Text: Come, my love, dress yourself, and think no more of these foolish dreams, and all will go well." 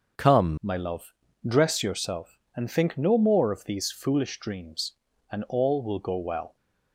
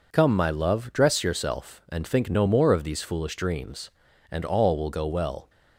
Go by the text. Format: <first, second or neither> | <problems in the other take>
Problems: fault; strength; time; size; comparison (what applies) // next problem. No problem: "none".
second | changes voice at "my"; from 0.6 s on; 5.9 s long